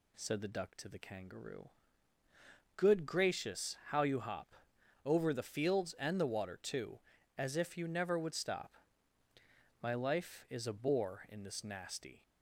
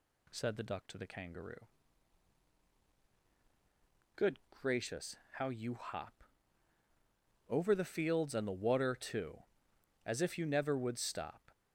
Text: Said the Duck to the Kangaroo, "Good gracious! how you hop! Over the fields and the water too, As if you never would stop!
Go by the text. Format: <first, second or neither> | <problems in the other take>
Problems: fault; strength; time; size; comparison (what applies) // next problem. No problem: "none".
second | goes on to say "My life is a bore in this nasty"; strong; from 9.8 s on; 2.4 s long